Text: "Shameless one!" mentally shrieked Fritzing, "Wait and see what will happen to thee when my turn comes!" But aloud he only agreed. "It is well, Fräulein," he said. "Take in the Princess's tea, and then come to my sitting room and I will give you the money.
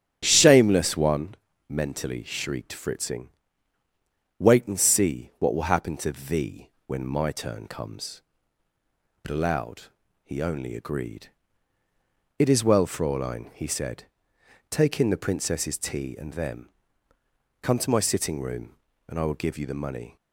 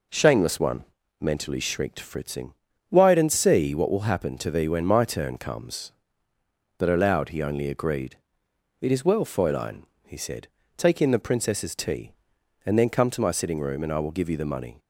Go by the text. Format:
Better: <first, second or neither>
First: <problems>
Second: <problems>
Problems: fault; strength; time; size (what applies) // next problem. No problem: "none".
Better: second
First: starts louder than the rest; strong; until 1.2 s; 10 dB // pauses between "thee" and "when"; slight; at 6.6 s; 0.16 s long // pauses between "aloud" and "he"; slight; at 9.9 s; 0.32 s long // says "them" for "then"; at 16.3 s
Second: none